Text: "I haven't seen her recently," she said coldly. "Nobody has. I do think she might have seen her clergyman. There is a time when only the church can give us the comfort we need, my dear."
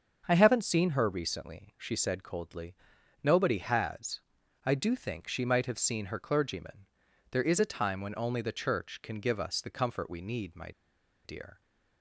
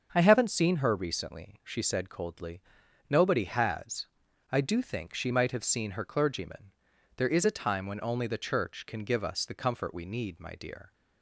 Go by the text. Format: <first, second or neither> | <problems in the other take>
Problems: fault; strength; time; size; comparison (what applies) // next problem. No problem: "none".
second | starts louder than the rest; until 1.2 s; 7 dB; also in the second // pauses between "my" and "dear"; noticeable; at 10.7 s; 0.54 s long